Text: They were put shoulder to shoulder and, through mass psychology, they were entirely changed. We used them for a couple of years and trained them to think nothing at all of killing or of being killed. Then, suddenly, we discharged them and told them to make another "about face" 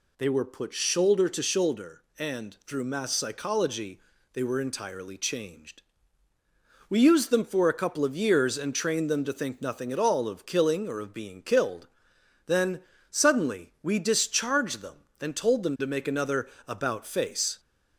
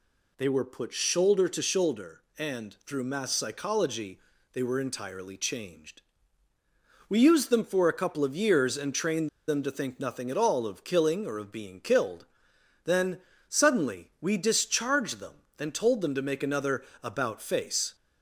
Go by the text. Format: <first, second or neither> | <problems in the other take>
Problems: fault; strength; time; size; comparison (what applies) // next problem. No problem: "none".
first | pauses between "trained" and "them"; slight; at 9.2 s; 0.19 s long // pauses between "another" and "about"; slight; at 16.8 s; 0.20 s long; slight in the first